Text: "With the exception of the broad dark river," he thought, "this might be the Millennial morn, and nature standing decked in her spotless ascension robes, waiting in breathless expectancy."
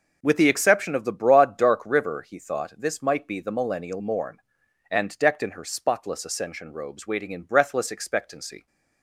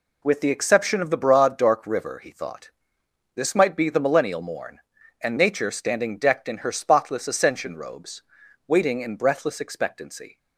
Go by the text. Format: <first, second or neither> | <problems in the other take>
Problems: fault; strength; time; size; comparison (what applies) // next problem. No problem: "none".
second | skips "nature standing"; at 5.1 s